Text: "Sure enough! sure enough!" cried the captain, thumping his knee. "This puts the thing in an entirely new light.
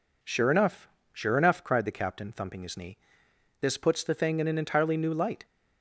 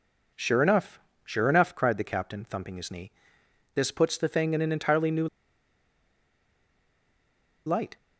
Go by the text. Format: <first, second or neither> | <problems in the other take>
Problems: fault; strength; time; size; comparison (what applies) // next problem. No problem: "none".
first | pauses between "new" and "light"; strong; at 5.2 s; 2.3 s long